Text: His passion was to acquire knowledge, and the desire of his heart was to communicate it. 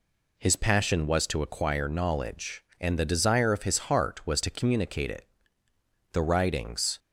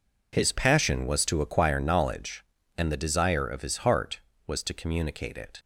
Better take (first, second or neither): second